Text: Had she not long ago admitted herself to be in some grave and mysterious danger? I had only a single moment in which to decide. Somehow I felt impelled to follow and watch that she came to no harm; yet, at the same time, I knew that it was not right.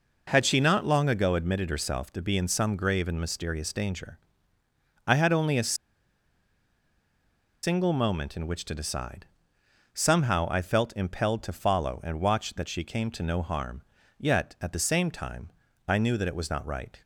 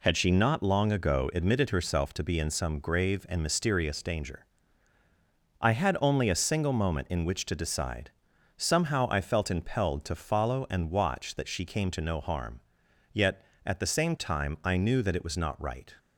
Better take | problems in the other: second | pauses between "a" and "single"; strong; at 5.7 s; 1.8 s long

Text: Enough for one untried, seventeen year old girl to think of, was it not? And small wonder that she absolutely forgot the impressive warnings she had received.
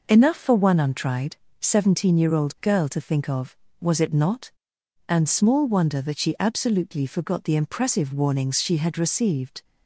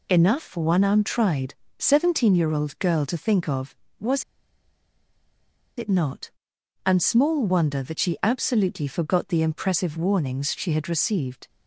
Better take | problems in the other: first | pauses between "was" and "it"; strong; at 4.2 s; 1.5 s long

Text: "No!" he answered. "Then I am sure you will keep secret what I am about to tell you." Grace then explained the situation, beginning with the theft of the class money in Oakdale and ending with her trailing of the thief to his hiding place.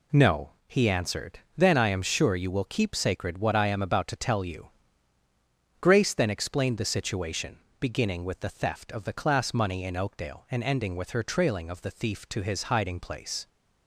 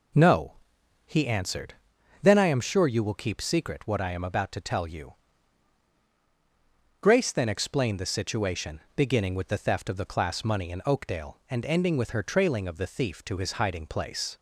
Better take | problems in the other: second | says "sacred" for "secret"; at 2.9 s

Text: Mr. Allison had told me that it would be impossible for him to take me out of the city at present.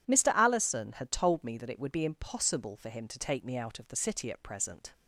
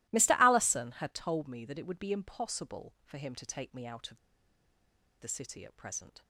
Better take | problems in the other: first | pauses between "of" and "the"; at 4.1 s; 1.0 s long

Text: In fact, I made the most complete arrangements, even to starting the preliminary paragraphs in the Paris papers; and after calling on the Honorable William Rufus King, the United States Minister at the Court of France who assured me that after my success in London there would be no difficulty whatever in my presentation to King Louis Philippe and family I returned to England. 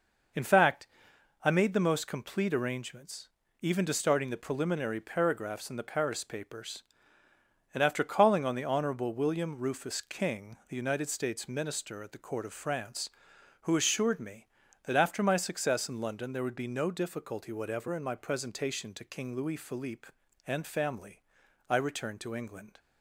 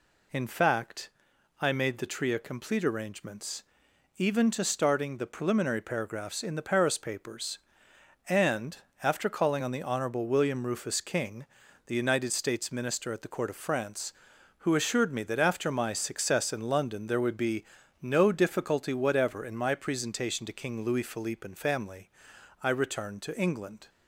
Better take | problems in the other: first | says "tria" for "most"; at 2.0 s // pauses between "and" and "after"; slight; at 8.7 s; 0.26 s long // pauses between "be" and "no"; at 17.6 s; 0.38 s long // pauses between "family" and "I"; noticeable; at 22.0 s; 0.54 s long; noticeable in the first

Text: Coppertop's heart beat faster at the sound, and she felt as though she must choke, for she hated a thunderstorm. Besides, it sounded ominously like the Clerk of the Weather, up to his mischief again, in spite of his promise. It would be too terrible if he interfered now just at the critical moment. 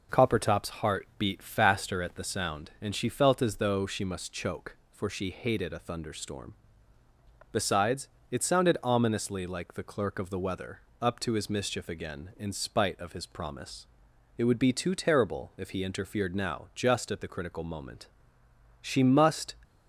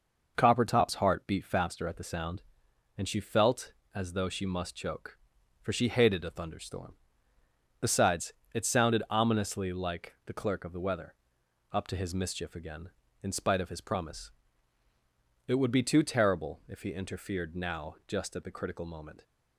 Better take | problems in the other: second | goes on to say "She must"; noticeable; from 18.8 s on; 0.72 s long

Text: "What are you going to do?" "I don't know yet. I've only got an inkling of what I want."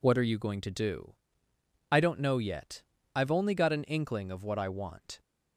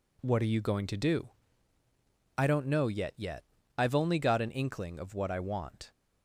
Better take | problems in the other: first | says "yet" twice; at 3.1 s

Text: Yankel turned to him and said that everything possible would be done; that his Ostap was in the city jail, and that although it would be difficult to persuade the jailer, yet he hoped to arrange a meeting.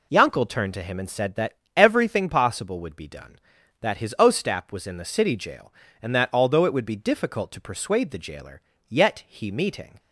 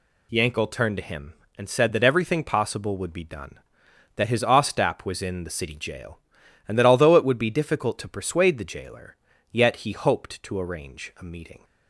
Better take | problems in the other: second | pauses between "that" and "everything"; slight; at 1.5 s; 0.18 s long // skips "hoped to arrange a"; at 9.5 s

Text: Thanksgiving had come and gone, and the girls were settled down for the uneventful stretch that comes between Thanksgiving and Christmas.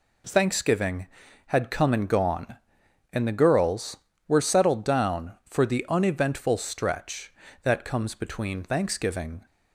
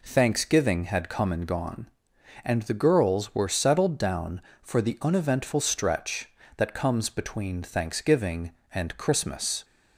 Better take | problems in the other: second | stops before "and Christmas"; at 9.4 s

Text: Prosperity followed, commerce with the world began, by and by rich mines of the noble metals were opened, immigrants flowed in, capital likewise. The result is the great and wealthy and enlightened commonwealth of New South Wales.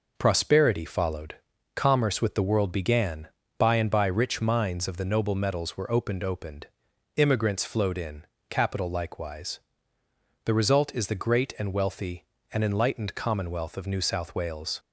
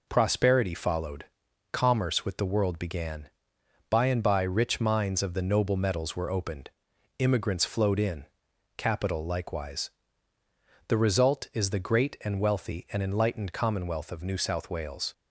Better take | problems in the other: second | says "opened" twice; at 6.2 s

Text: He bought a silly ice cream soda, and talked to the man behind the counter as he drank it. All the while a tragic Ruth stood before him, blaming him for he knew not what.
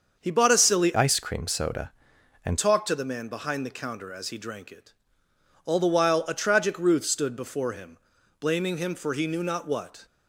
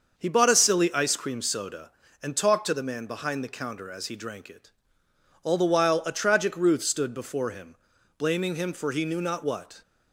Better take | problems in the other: second | starts louder than the rest; until 1.2 s; 6.5 dB; also in the second // changes voice from "ice" to "and"; from 0.9 to 2.5 s; 1.6 s long

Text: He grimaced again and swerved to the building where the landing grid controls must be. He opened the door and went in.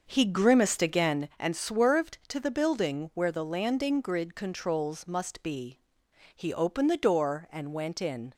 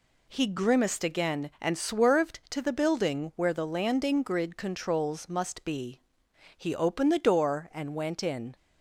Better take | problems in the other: second | starts louder than the rest; until 1.4 s; 6.5 dB

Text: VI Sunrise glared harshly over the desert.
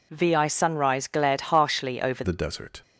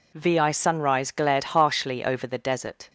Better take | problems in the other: second | changes voice at "the"; from 2.2 s on; 0.6 s long

